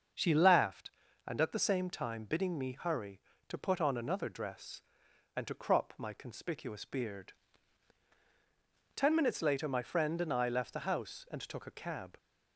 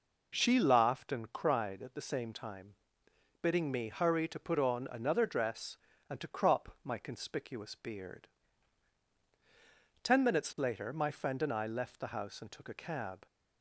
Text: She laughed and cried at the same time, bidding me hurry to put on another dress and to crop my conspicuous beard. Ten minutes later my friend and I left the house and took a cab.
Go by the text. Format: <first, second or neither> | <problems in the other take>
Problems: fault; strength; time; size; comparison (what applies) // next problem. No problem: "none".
second | starts louder than the rest; until 1.5 s; 6.5 dB // skips "cried"; at 1.4 s